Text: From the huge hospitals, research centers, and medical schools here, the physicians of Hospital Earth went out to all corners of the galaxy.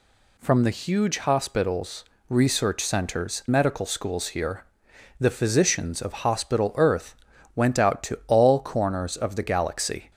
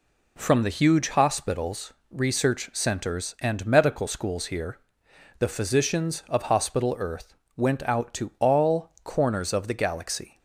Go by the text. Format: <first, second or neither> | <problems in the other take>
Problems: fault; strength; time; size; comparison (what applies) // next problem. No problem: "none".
second | skips "and"; at 3.4 s // pauses between "Earth" and "went"; at 7.1 s; 0.40 s long; slight in the second